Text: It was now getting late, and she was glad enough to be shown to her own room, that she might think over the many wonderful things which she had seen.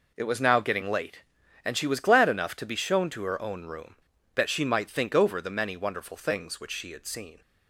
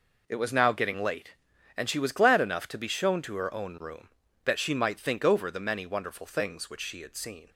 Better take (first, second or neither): neither